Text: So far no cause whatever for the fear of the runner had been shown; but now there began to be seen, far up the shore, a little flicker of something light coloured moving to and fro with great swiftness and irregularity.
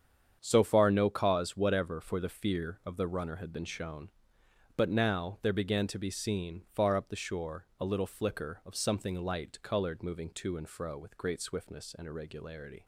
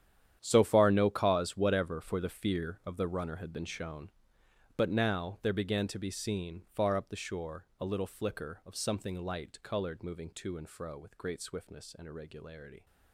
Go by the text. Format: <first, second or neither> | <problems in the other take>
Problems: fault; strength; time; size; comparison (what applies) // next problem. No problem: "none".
first | gets quieter; strong; throughout; 15 dB // starts louder than the rest; strong; until 1.4 s; 10 dB; strong in the first